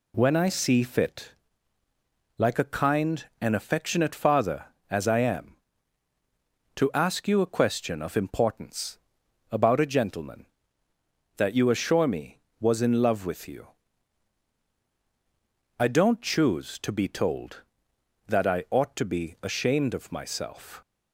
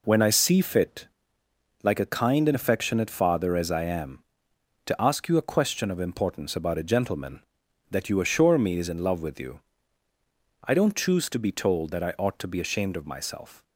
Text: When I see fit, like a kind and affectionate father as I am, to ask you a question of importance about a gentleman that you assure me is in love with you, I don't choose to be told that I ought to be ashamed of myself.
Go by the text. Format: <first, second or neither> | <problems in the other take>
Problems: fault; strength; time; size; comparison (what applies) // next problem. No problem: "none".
second | pauses between "importance" and "about"; noticeable; at 8.9 s; 0.50 s long // says "was" for "is"; at 12.5 s